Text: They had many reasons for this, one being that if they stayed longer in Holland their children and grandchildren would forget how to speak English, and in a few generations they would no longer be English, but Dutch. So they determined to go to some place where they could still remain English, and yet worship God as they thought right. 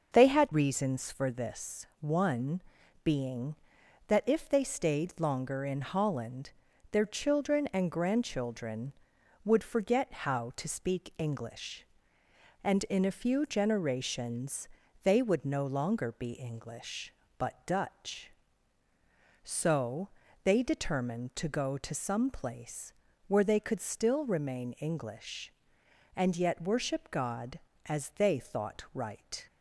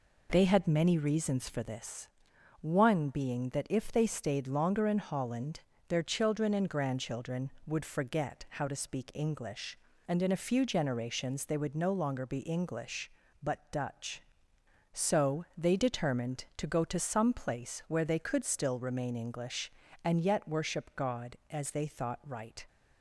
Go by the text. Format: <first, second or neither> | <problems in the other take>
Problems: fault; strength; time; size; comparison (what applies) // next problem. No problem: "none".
second | starts louder than the rest; until 1.1 s; 6.5 dB // skips "many"; at 0.5 s // pauses between "one" and "being"; at 2.6 s; 0.44 s long // pauses between "Holland" and "their"; at 6.5 s; 0.40 s long; slight in the second // pauses between "generations" and "they"; at 14.6 s; 0.38 s long // pauses between "So" and "they"; slight; at 20.0 s; 0.34 s long // pauses between "place" and "where"; slight; at 22.9 s; 0.36 s long